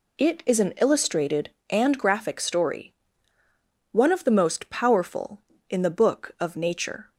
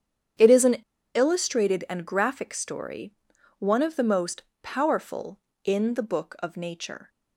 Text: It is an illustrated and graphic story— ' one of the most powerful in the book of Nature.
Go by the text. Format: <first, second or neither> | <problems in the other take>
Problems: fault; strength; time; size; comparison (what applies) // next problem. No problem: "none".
first | starts louder than the rest; strong; until 1.7 s; 8.5 dB // pauses between "an" and "illustrated"; at 0.7 s; 0.41 s long // pauses between "most" and "powerful"; slight; at 4.4 s; 0.18 s long